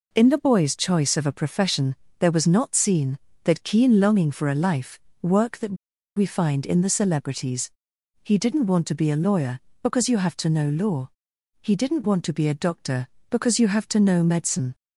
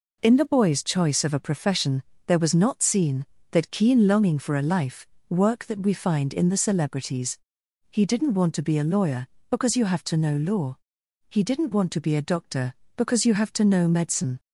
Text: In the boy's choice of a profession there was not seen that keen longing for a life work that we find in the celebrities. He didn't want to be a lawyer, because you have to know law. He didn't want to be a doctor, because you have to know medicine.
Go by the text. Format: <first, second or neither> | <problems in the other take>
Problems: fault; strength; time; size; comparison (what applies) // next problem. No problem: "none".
second | pauses between "profession" and "there"; slight; at 1.9 s; 0.24 s long; slight in the second // pauses between "life" and "work"; slight; at 4.9 s; 0.24 s long; slight in the second // pauses between "that" and "we"; at 5.7 s; 0.41 s long